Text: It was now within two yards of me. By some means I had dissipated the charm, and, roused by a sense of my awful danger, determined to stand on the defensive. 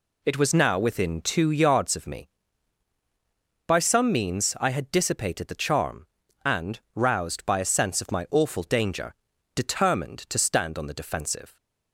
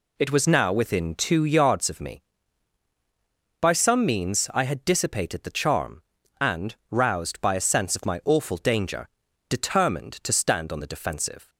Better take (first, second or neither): neither